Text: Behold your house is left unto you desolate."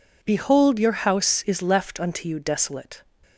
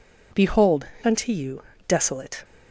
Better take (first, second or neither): first